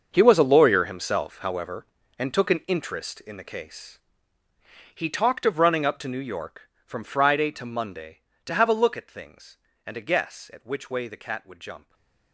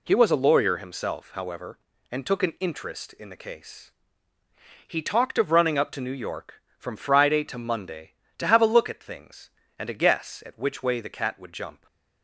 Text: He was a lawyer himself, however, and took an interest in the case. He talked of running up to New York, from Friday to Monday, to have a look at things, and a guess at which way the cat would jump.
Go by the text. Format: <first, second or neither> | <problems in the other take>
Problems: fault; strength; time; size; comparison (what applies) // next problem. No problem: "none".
second | gets quieter; strong; throughout; 15 dB // stays silent after the last word; slight; from 11.7 s on; 0.6 s long